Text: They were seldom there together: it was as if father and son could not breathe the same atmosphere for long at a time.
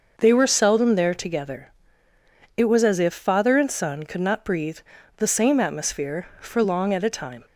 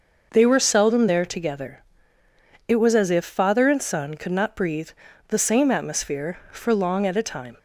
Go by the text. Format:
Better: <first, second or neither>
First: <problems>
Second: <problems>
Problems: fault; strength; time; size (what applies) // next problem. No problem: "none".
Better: neither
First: starts louder than the rest; noticeable; until 1.1 s; 6 dB // pauses between "breathe" and "the"; at 4.7 s; 0.38 s long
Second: starts louder than the rest; noticeable; until 1.3 s; 6 dB // pauses between "breathe" and "the"; at 4.8 s; 0.38 s long